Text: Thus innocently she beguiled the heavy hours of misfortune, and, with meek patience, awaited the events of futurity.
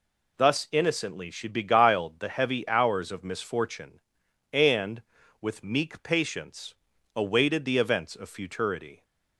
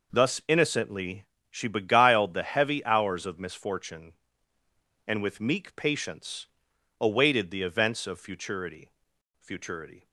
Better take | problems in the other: first | pauses between "innocently" and "she"; slight; at 1.2 s; 0.24 s long // says "futurity" twice; at 9.3 s

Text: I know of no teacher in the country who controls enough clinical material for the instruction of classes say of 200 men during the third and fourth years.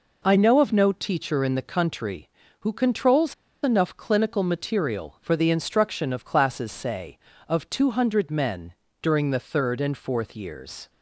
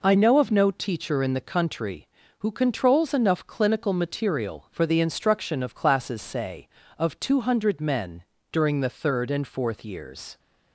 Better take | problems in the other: second | pauses between "controls" and "enough"; slight; at 3.3 s; 0.29 s long // pauses between "men" and "during"; slight; at 8.7 s; 0.26 s long; slight in the second

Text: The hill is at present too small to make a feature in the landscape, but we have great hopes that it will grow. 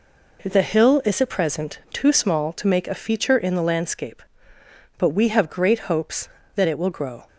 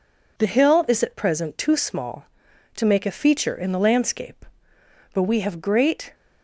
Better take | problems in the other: first | stops before "hopes that it will grow"; at 6.1 s

